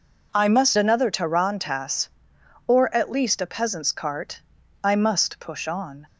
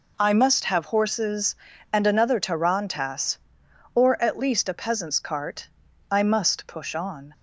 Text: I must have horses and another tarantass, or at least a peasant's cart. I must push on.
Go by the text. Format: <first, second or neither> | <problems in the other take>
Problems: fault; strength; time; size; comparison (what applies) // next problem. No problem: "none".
second | skips "have horses and"; at 0.7 s